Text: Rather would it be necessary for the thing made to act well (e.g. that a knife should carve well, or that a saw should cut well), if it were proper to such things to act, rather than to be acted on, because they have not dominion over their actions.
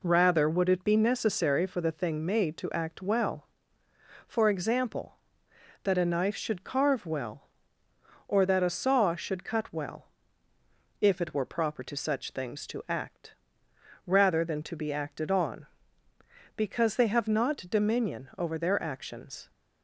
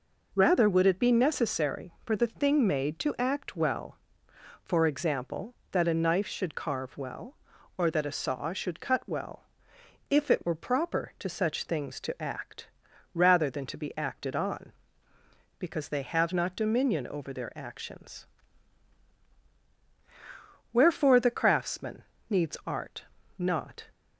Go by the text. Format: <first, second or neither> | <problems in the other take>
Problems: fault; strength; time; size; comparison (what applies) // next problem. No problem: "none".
first | goes on to say "Wherefore the craftsman needs art not"; strong; from 20.7 s on; 3.1 s long